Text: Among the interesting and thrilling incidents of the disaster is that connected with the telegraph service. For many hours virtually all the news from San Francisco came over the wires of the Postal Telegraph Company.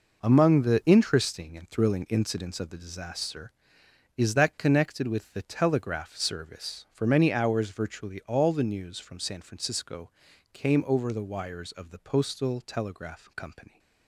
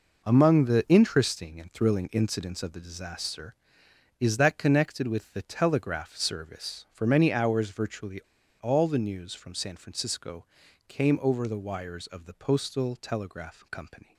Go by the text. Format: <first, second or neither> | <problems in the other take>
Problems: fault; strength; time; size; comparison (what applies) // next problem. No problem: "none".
first | pauses between "virtually" and "all"; at 8.2 s; 0.41 s long // pauses between "Francisco" and "came"; at 10.4 s; 0.42 s long; also in the first